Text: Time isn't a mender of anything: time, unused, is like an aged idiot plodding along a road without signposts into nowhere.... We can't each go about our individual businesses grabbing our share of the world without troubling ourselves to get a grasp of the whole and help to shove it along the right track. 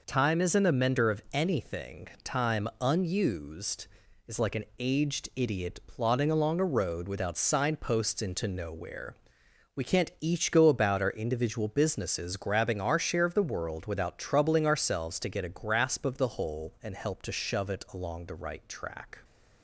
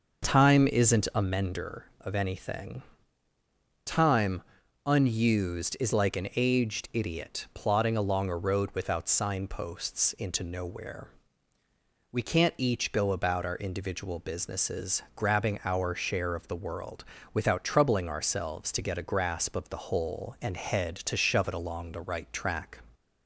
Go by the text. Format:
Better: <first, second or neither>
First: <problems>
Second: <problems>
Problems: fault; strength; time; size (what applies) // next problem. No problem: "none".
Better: first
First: none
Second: pauses between "world" and "without"; slight; at 17.0 s; 0.30 s long // says "head" for "help"; at 20.5 s